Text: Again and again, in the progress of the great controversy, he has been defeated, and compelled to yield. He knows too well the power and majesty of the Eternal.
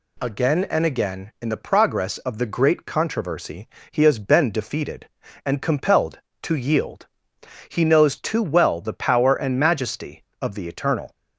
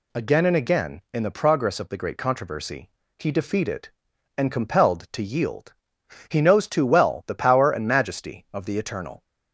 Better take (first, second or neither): first